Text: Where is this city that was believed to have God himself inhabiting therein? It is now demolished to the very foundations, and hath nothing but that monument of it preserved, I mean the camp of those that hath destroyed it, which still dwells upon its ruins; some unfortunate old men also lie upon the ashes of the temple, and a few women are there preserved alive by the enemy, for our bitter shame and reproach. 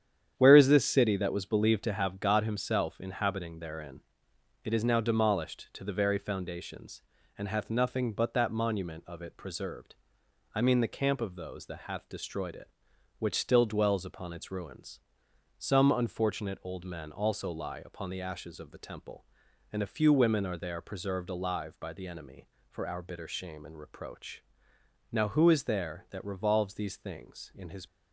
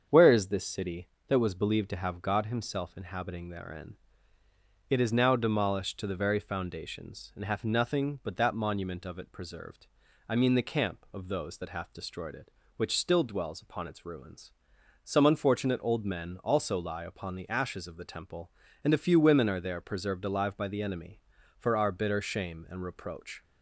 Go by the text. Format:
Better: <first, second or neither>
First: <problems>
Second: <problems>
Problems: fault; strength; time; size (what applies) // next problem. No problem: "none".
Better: second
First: starts louder than the rest; strong; until 1.4 s; 9 dB // goes on to say "Now who is there that revolves these things in his"; strong; from 25.1 s on; 2.7 s long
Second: starts louder than the rest; until 1.1 s; 7 dB